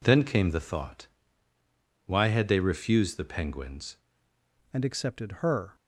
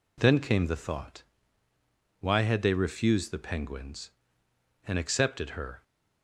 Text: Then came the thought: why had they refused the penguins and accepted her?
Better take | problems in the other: second | changes voice at "and"; from 4.7 s on; 1.0 s long

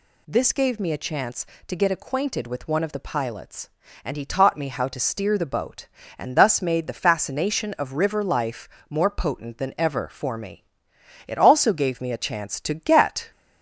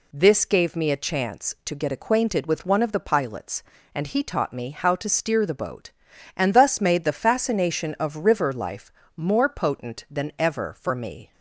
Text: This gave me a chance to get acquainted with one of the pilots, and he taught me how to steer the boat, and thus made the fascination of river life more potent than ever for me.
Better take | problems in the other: second | pauses between "life" and "more"; slight; at 8.6 s; 0.20 s long; slight in the second // goes on to say "It also gave me a chance to get"; strong; from 11.2 s on; 2.0 s long

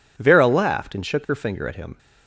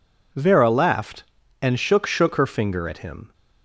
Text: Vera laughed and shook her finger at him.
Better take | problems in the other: first | says "shook" twice; at 2.0 s

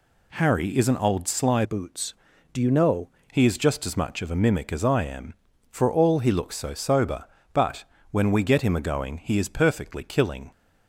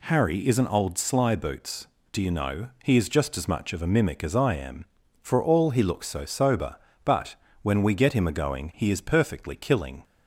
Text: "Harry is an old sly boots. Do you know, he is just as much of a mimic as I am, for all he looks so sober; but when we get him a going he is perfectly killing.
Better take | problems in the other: second | changes voice from "boots" to "know"; from 1.6 to 3.0 s; 1.4 s long // pauses between "but" and "when"; slight; at 7.8 s; 0.26 s long; slight in the second

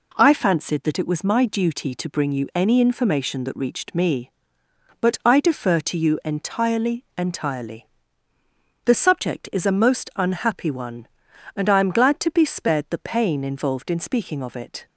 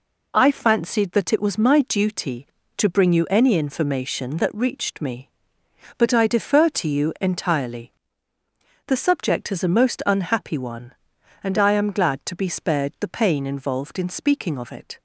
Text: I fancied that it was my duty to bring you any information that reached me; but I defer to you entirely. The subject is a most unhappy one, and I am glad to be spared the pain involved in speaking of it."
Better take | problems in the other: second | says "entirely" twice; at 7.1 s

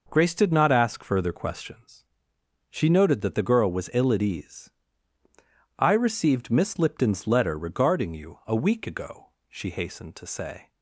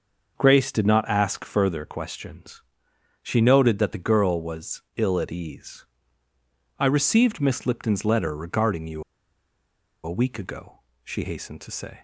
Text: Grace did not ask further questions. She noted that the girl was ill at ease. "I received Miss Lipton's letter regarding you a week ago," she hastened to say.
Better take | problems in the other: first | starts louder than the rest; noticeable; until 1.3 s; 6 dB // pauses between "was" and "ill"; slight; at 4.8 s; 0.16 s long // pauses between "you" and "a"; at 9.0 s; 1.0 s long

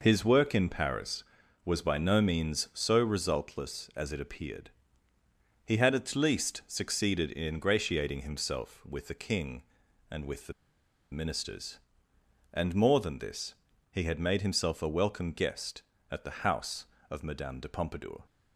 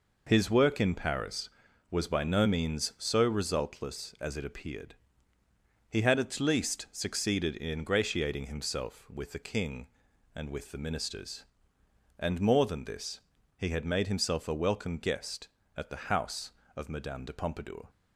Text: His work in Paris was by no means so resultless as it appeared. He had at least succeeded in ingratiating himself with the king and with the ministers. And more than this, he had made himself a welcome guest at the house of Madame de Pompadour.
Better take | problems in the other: second | pauses between "the" and "ministers"; noticeable; at 10.5 s; 0.59 s long

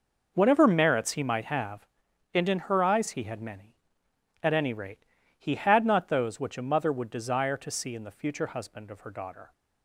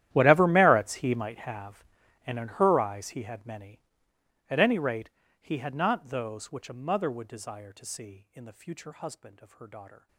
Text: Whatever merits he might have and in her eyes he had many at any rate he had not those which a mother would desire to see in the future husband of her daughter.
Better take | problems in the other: first | gets quieter; strong; throughout; 21 dB // pauses between "rate" and "he"; slight; at 5.0 s; 0.30 s long; slight in the first

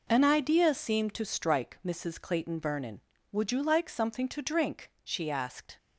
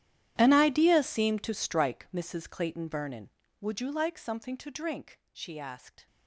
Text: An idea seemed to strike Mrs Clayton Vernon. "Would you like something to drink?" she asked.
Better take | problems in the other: first | gets quieter; strong; throughout; 20 dB

